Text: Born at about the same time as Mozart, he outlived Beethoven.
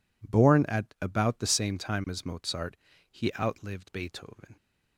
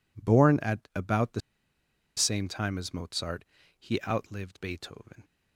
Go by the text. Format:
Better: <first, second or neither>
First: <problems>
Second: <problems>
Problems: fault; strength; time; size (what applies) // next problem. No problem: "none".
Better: first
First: none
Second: pauses between "the" and "same"; noticeable; at 1.3 s; 0.76 s long